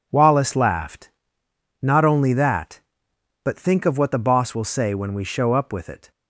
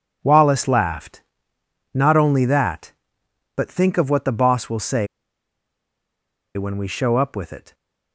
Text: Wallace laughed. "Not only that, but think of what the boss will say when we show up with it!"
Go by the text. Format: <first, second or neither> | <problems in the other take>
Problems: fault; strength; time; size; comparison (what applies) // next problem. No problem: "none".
first | pauses between "say" and "when"; strong; at 5.0 s; 1.4 s long